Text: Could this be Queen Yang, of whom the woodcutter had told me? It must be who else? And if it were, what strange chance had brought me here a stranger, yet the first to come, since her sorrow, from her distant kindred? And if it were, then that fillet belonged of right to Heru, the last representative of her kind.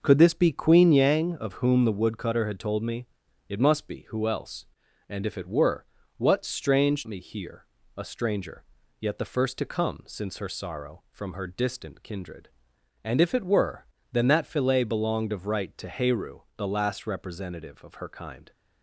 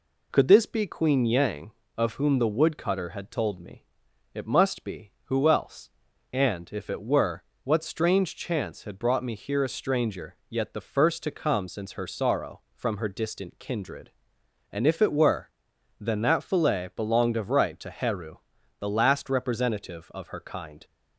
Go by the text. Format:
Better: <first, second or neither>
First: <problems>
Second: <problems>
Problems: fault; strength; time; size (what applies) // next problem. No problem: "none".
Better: second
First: starts louder than the rest; noticeable; until 1.0 s; 6 dB // skips "chance had brought"; at 7.0 s // pauses between "here" and "a"; slight; at 7.6 s; 0.32 s long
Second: none